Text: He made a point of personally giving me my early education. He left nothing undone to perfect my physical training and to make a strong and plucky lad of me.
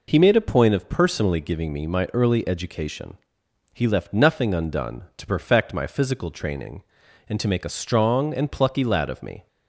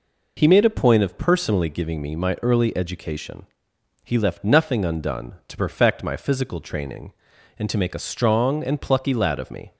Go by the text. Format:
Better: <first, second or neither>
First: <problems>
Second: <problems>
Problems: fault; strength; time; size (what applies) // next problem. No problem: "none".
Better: neither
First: none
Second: none